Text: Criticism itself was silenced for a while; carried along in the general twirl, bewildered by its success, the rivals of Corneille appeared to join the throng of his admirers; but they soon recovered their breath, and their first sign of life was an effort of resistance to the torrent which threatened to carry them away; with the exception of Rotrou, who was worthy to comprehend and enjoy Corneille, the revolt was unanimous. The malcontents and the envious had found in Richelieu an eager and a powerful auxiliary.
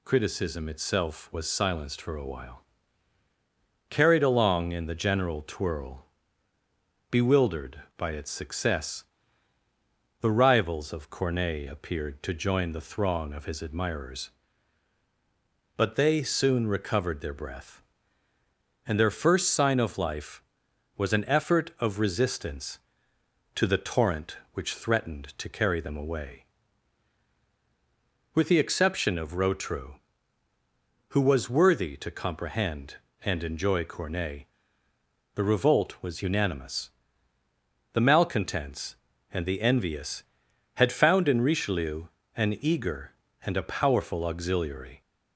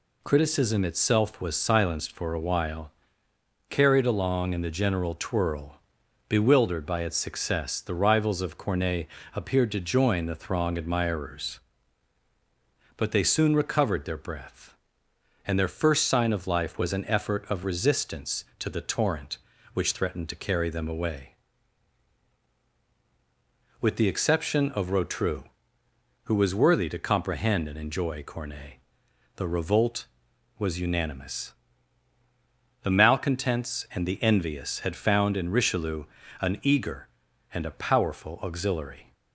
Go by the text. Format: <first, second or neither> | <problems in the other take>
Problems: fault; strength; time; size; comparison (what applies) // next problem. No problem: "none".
first | pauses between "Corneille" and "appeared"; slight; at 9.0 s; 0.30 s long // skips "of his"; at 10.7 s // pauses between "Richelieu" and "an"; slight; at 36.0 s; 0.36 s long; slight in the first